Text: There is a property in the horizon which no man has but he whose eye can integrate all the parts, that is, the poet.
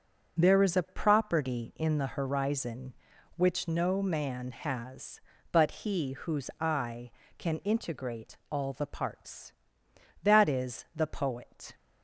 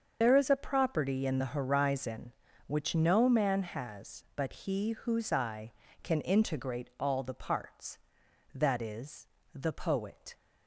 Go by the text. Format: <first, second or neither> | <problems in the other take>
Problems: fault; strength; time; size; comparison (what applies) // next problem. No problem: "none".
first | loses the start of "There"; at 0.2 s; 45 ms // starts louder than the rest; until 1.2 s; 6.5 dB